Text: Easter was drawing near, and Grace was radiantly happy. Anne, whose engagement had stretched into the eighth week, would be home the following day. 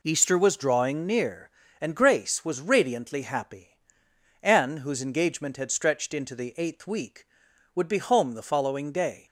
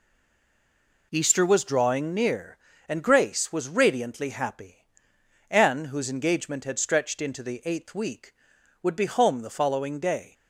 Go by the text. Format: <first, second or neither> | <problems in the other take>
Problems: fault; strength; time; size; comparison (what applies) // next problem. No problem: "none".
first | stays silent before the first word; until 1.1 s; 1.1 s long